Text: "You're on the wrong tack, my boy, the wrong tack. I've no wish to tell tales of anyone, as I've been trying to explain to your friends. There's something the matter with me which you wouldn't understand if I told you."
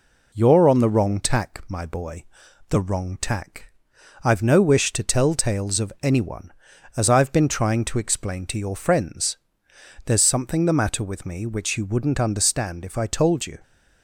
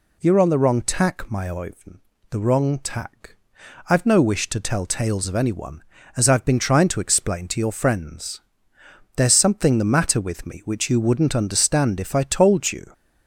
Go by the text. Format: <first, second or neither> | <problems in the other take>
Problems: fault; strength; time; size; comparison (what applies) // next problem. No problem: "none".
first | says "oivn" for "boy"; at 1.4 s